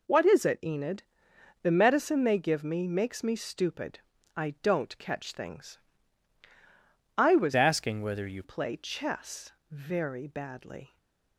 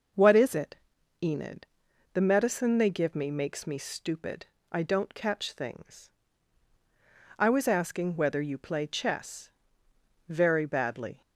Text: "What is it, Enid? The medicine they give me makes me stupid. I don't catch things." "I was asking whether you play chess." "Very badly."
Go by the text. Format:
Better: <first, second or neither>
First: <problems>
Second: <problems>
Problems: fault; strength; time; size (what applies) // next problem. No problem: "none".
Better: second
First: changes voice from "asking" to "you"; from 7.5 to 8.4 s; 0.9 s long // stays silent after the last word; slight; from 10.8 s on; 0.5 s long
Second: none